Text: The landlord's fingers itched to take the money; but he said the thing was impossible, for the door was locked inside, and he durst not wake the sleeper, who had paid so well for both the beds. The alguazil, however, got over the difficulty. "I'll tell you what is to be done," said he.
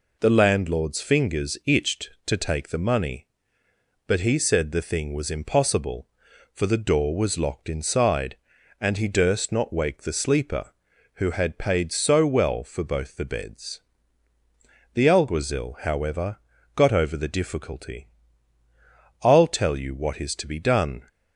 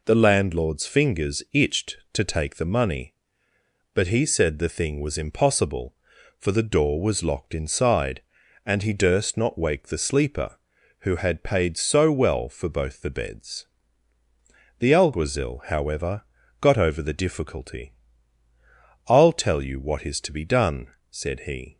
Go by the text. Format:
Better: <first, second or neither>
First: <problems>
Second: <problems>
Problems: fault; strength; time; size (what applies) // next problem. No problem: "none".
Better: second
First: stops before "said he"; at 21.0 s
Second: none